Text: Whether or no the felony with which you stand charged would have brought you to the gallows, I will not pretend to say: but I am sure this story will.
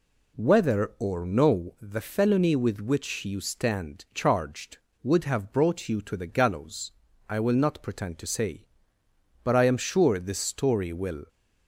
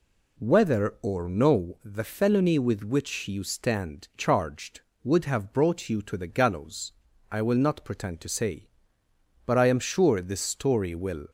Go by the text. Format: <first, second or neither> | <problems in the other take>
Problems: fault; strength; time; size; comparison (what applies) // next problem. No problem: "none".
neither | none